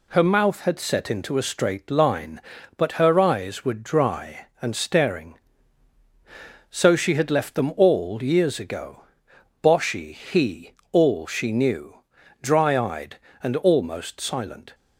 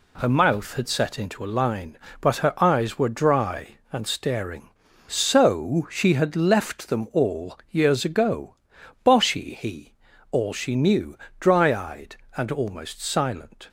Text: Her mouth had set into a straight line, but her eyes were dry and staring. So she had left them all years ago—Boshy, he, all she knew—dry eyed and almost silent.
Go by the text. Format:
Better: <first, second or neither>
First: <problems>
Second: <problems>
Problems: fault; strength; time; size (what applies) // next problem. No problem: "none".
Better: first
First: none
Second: skips "straight"; at 1.5 s